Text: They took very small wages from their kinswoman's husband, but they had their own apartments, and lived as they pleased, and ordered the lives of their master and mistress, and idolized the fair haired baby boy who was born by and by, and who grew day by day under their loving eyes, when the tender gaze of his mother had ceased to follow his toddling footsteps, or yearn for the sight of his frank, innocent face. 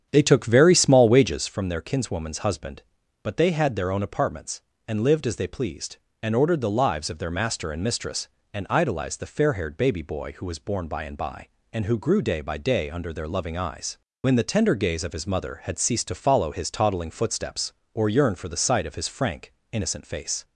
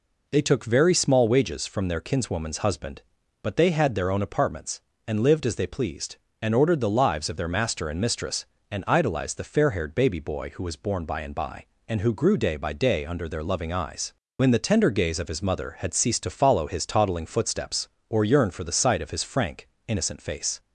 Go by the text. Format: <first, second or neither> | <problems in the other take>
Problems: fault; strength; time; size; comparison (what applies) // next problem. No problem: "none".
second | starts louder than the rest; strong; until 1.6 s; 8.5 dB